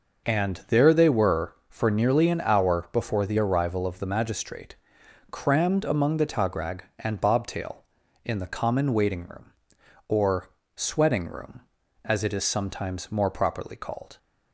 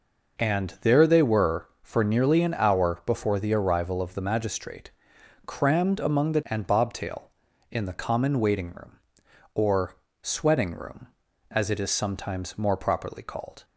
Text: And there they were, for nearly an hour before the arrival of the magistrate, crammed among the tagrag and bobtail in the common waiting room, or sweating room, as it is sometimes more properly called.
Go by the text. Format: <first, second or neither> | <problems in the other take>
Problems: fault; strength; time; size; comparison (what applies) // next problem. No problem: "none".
first | skips "tagrag"; at 6.4 s // pauses between "or" and "sweating"; slight; at 9.9 s; 0.26 s long; slight in the first